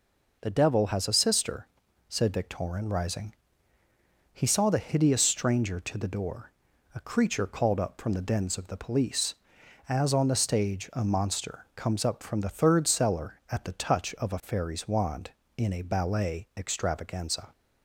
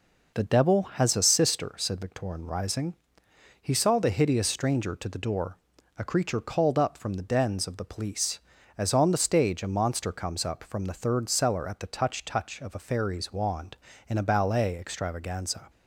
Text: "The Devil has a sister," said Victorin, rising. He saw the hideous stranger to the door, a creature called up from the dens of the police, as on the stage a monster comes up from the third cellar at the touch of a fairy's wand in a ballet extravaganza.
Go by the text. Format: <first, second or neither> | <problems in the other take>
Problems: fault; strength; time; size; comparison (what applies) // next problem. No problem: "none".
first | says "touch" twice; at 12.2 s